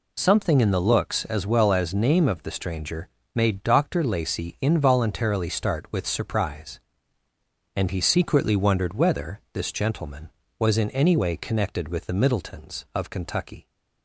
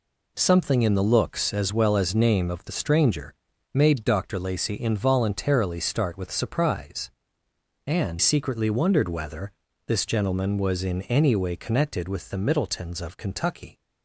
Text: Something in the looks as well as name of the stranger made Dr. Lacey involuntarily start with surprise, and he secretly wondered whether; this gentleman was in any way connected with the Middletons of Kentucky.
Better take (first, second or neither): first